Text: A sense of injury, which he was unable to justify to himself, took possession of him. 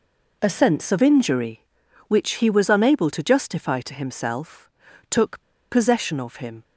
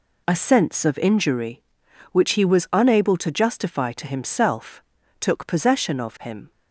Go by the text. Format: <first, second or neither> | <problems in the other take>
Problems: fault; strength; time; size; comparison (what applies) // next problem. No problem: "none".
second | pauses between "took" and "possession"; slight; at 5.4 s; 0.27 s long